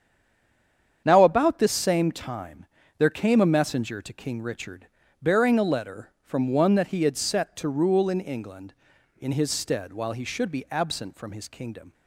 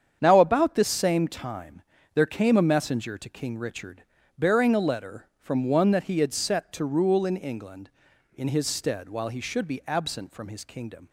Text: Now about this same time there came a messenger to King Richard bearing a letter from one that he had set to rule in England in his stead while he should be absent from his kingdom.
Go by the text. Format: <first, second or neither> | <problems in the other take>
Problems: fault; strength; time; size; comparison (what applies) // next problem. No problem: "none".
second | stays silent before the first word; until 1.0 s; 1.0 s long // starts louder than the rest; strong; until 2.0 s; 8 dB; strong in the second // pauses between "time" and "there"; slight; at 2.6 s; 0.32 s long; slight in the second // pauses between "Richard" and "bearing"; slight; at 4.8 s; 0.36 s long; slight in the second